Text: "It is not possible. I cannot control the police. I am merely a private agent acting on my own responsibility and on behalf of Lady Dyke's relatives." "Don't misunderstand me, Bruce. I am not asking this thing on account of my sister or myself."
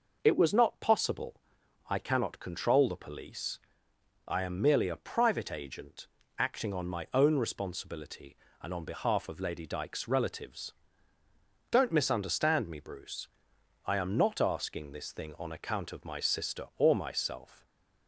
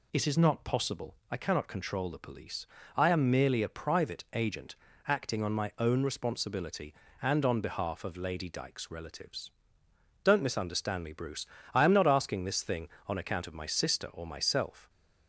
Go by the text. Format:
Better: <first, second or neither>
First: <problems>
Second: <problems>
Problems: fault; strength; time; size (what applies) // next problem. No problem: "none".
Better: second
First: says "was" for "is"; at 0.3 s // pauses between "agent" and "acting"; slight; at 6.0 s; 0.30 s long // stays silent after the last word; slight; from 17.5 s on; 0.5 s long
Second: pauses between "agent" and "acting"; slight; at 4.7 s; 0.30 s long